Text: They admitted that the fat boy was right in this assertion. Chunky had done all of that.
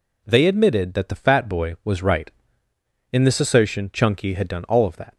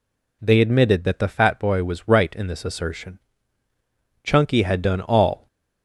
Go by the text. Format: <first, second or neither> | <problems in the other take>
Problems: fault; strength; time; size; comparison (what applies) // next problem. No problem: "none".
first | stops before "of that"; at 5.4 s